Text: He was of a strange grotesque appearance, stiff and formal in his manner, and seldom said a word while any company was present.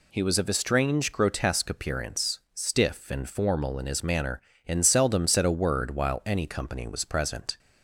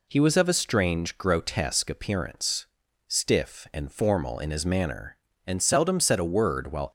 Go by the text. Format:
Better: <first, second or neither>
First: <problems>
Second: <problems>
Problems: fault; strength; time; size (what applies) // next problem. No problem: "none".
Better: first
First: none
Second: stops before "any company was present"; at 6.8 s